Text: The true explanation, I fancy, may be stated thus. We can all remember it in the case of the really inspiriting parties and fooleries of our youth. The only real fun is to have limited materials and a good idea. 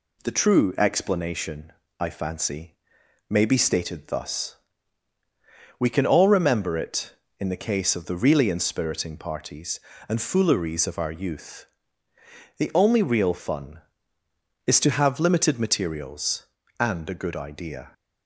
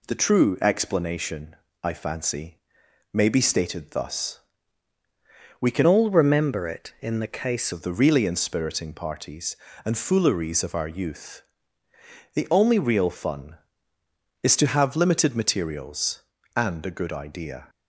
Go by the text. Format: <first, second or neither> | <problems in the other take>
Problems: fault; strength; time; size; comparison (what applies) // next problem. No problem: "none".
first | changes voice from "all" to "case"; from 5.8 to 7.7 s; 1.9 s long